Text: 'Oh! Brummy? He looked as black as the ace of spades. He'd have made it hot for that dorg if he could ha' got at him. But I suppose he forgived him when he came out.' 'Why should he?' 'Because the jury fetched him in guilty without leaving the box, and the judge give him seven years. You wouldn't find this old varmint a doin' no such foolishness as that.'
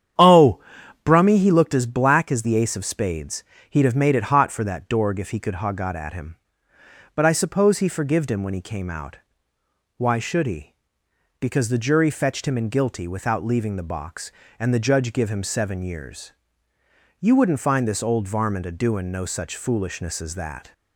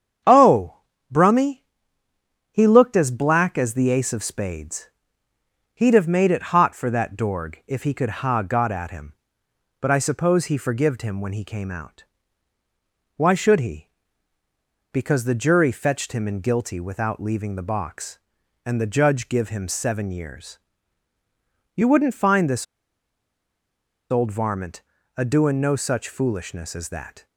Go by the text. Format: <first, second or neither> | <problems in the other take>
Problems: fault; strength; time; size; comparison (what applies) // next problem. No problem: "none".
first | starts louder than the rest; strong; until 1.5 s; 8 dB; strong in the first // pauses between "this" and "old"; strong; at 22.6 s; 1.4 s long // pauses between "varmint" and "a"; at 24.7 s; 0.38 s long